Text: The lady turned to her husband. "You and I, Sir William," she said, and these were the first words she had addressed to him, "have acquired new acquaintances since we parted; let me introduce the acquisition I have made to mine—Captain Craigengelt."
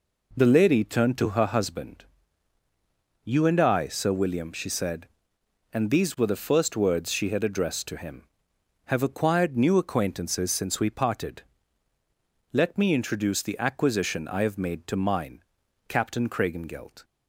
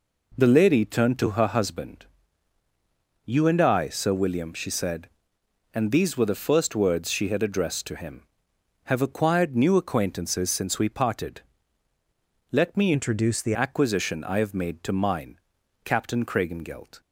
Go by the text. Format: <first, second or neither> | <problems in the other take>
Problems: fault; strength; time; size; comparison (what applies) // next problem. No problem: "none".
first | changes voice from "introduce" to "the"; from 12.9 to 13.5 s; 0.6 s long